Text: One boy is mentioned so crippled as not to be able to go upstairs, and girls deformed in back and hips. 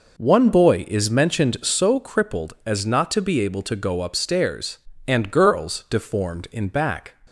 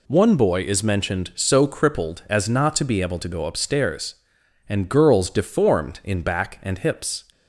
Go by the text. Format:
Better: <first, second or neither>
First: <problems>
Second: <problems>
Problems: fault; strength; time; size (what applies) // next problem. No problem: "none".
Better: second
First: stops before "and hips"; at 7.2 s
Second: none